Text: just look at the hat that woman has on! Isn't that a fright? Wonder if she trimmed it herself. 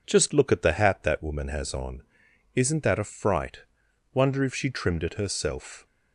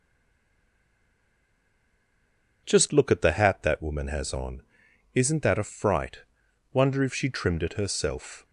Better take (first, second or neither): first